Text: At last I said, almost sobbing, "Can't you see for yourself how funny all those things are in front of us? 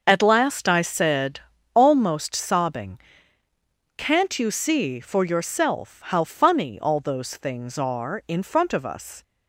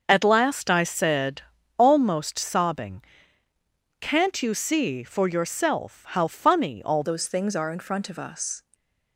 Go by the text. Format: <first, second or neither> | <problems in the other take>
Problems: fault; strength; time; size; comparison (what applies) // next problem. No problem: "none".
first | starts louder than the rest; noticeable; until 1.0 s; 6 dB; also in the first // changes voice at "those"; from 7.0 s on; 1.6 s long // stays silent after the last word; slight; from 8.6 s on; 0.5 s long